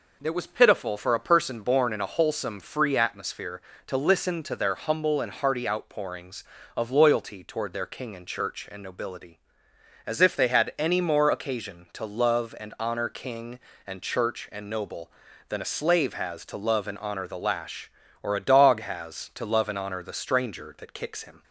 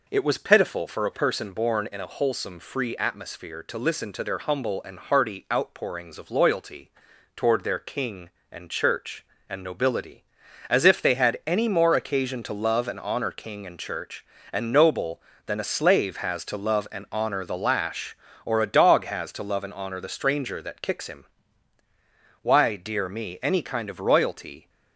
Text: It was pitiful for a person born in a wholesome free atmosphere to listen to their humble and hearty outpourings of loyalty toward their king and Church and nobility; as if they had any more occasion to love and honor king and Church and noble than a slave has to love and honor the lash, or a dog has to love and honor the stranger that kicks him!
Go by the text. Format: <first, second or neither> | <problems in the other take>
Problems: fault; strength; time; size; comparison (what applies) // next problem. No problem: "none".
first | pauses between "loyalty" and "toward"; at 6.9 s; 0.44 s long // goes on to say "Why dear me any kind of royalty"; strong; from 22.4 s on; 2.2 s long